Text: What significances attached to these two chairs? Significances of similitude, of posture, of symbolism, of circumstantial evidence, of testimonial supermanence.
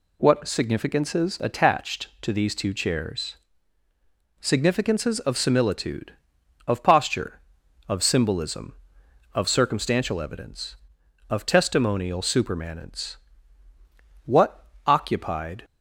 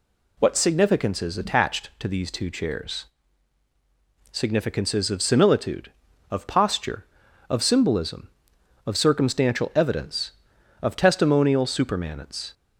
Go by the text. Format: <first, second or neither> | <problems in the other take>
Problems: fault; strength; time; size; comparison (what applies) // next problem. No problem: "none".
second | goes on to say "What occupied"; from 14.2 s on; 1.3 s long